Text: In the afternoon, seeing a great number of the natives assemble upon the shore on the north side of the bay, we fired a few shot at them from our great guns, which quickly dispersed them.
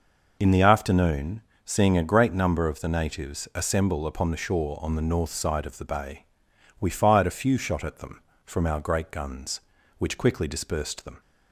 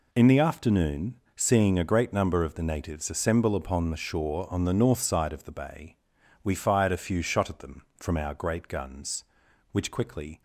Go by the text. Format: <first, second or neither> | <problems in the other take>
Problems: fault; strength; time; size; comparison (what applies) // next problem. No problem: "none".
first | stops before "dispersed them"; at 10.3 s